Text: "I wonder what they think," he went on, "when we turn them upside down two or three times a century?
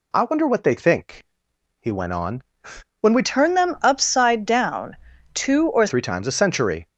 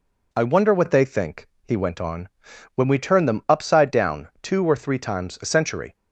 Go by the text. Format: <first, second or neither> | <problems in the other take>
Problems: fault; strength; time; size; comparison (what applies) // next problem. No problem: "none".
second | changes voice from "turn" to "or"; from 3.2 to 5.8 s; 2.6 s long // pauses between "down" and "two"; slight; at 4.9 s; 0.36 s long; slight in the second